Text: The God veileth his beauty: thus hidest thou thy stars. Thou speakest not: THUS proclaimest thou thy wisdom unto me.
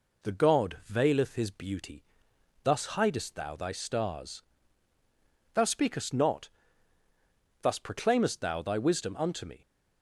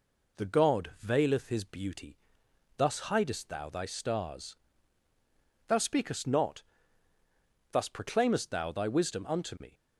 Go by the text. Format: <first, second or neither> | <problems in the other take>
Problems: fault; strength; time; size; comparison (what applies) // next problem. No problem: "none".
neither | none